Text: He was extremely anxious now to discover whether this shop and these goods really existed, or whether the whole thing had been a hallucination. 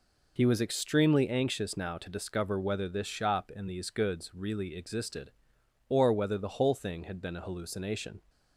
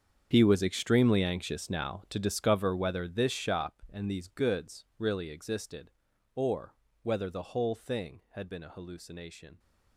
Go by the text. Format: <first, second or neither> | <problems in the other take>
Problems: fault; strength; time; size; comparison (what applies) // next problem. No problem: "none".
first | gets quieter; strong; throughout; 16 dB // pauses between "or" and "whether"; slight; at 6.7 s; 0.28 s long